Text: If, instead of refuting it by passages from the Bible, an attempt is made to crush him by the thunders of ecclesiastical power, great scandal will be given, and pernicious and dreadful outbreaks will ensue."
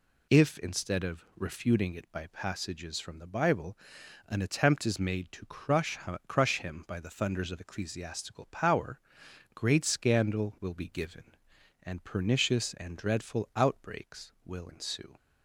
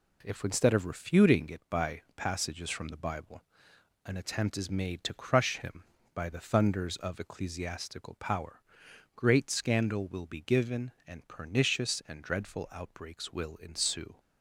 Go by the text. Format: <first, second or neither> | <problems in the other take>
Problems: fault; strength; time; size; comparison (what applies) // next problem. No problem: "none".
second | says "crush" twice; at 6.2 s